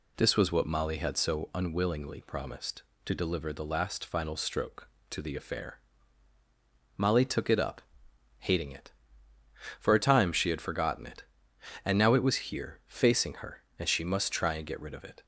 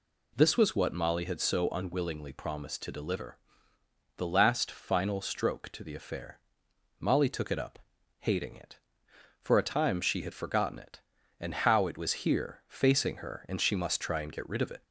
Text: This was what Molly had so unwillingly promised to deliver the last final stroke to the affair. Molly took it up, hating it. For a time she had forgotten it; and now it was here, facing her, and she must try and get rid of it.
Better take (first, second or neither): first